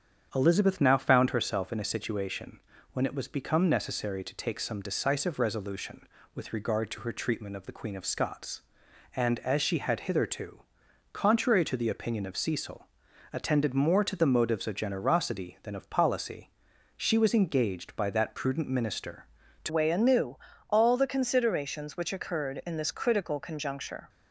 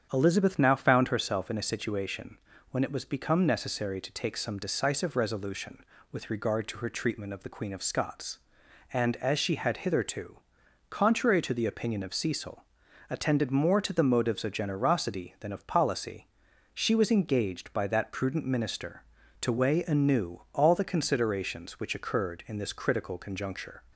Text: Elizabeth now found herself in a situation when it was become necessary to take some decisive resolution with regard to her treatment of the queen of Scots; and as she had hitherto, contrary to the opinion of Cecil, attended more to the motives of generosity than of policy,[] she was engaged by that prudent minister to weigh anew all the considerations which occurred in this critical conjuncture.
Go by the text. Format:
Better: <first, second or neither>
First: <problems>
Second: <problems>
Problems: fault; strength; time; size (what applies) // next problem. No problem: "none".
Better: second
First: starts louder than the rest; strong; until 1.3 s; 8 dB // pauses between "situation" and "when"; slight; at 2.5 s; 0.34 s long // changes voice at "weigh"; from 19.6 s on; 4.4 s long // pauses between "anew" and "all"; slight; at 20.3 s; 0.32 s long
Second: starts louder than the rest; strong; until 1.1 s; 8 dB // pauses between "situation" and "when"; slight; at 2.3 s; 0.34 s long